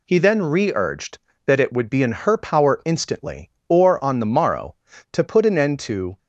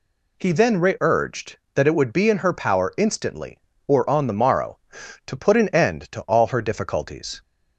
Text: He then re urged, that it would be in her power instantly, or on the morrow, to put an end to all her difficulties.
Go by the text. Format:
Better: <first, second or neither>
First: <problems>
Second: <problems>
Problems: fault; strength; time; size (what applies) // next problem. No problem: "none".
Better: second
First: stops before "all her difficulties"; at 6.1 s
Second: none